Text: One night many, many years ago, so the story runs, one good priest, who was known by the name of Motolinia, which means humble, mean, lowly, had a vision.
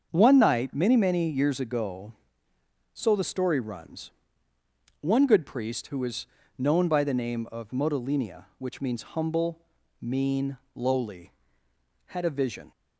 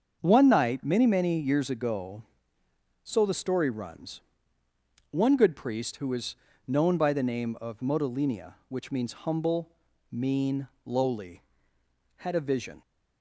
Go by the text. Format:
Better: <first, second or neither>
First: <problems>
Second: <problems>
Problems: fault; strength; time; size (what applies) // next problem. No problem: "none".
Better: neither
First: starts louder than the rest; until 1.1 s; 7 dB // pauses between "was" and "known"; slight; at 6.2 s; 0.32 s long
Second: starts louder than the rest; until 1.2 s; 7 dB // pauses between "was" and "known"; slight; at 6.3 s; 0.32 s long